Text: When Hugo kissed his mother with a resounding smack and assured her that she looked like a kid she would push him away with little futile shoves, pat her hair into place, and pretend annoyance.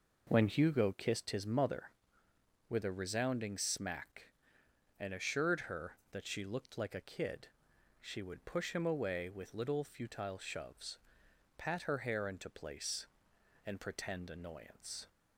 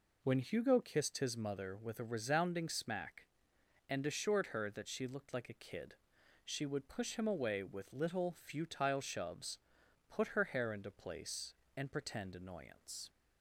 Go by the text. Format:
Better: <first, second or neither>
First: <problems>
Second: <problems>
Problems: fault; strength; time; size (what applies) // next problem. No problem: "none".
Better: first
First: pauses between "kid" and "she"; noticeable; at 7.4 s; 0.54 s long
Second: pauses between "kid" and "she"; noticeable; at 5.9 s; 0.50 s long // says "put" for "pat"; at 10.0 s